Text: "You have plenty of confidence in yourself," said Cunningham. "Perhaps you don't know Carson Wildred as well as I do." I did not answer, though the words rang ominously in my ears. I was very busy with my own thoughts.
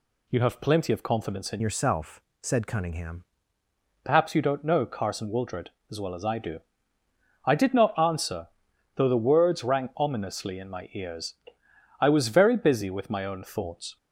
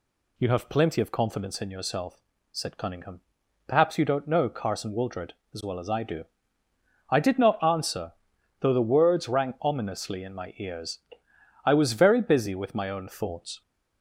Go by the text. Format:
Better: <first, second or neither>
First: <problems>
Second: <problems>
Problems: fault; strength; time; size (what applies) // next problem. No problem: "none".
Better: second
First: changes voice from "yourself" to "Cunningham"; from 1.5 to 3.2 s; 1.7 s long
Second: none